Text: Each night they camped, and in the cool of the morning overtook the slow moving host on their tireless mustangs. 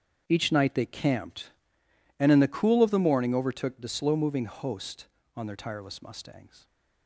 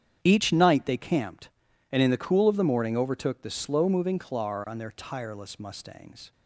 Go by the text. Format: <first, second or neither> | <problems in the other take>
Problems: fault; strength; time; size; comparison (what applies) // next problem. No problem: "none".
first | starts louder than the rest; strong; until 1.2 s; 9 dB; strong in the first // says "clar" for "host"; at 4.1 s